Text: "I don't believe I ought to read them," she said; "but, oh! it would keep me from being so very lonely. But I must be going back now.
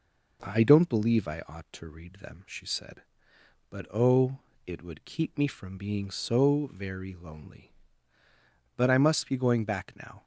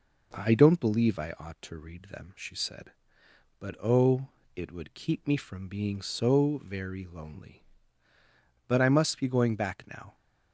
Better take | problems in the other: neither | none

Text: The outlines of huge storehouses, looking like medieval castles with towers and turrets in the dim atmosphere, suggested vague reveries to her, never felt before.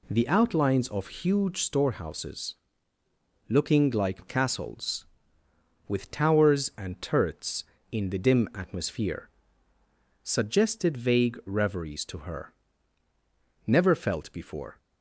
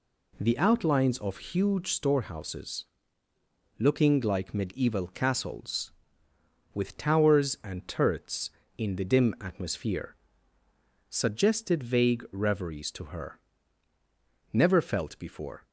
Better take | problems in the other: second | skips "medieval"; at 4.2 s

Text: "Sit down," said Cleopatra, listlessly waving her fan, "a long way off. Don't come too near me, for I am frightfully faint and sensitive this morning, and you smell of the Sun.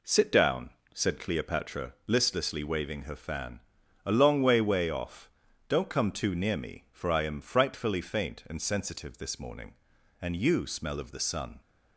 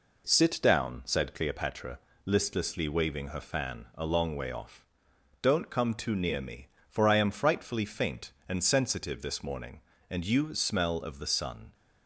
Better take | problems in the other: second | says "way" twice; at 4.5 s

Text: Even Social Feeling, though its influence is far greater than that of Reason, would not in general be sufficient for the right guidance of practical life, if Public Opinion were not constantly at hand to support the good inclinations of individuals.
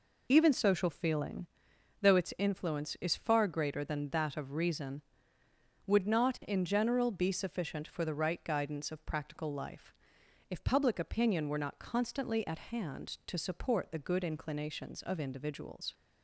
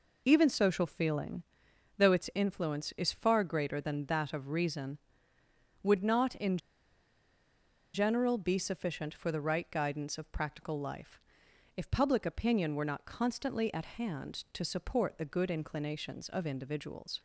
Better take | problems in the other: first | pauses between "in" and "general"; strong; at 6.5 s; 1.3 s long

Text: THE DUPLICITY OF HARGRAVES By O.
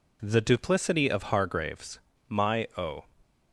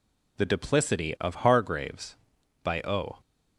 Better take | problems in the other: second | says "My" for "By"; at 2.2 s

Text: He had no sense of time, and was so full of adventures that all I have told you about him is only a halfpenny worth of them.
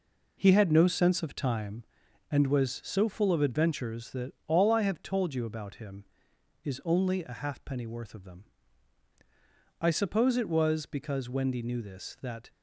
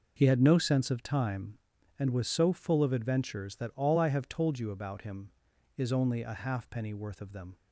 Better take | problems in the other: second | goes on to say "I suppose it was because Wendy knew this that"; strong; from 9.8 s on; 2.6 s long

